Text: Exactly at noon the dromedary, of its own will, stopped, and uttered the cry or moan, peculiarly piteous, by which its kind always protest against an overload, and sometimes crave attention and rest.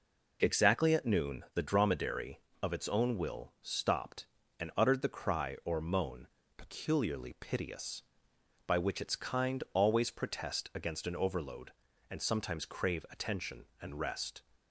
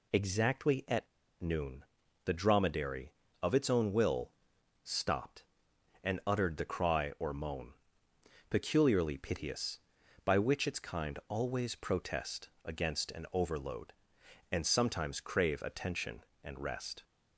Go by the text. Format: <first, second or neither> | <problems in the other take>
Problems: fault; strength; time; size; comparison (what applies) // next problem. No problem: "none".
first | pauses between "at" and "noon"; slight; at 1.0 s; 0.32 s long // pauses between "noon" and "the"; at 1.8 s; 0.40 s long